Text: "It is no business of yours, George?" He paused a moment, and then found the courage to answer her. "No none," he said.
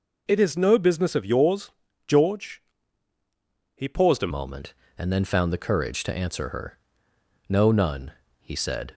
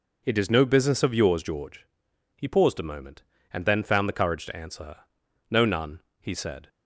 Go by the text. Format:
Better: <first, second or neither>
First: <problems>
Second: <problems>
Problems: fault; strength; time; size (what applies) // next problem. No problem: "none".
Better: second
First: changes voice at "moment"; from 4.3 s on; 4.6 s long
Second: none